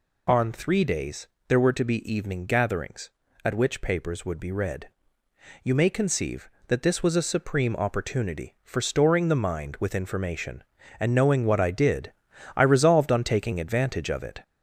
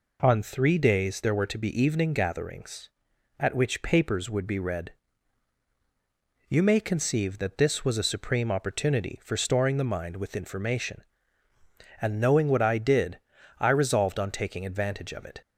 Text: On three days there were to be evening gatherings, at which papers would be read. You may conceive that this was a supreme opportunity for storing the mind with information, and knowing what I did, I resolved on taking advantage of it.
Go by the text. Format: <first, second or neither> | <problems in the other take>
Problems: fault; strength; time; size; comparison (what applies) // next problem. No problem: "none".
second | gets louder; slight; throughout; 2.5 dB // pauses between "days" and "there"; slight; at 1.2 s; 0.22 s long